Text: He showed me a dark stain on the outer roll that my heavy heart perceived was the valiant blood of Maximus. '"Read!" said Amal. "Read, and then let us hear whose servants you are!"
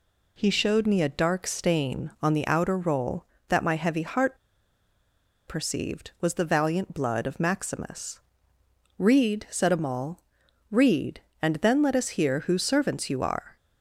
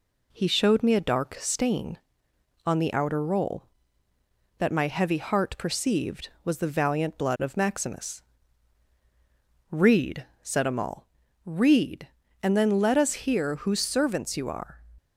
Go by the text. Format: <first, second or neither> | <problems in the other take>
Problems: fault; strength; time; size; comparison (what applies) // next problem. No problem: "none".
second | pauses between "heart" and "perceived"; at 4.3 s; 1.1 s long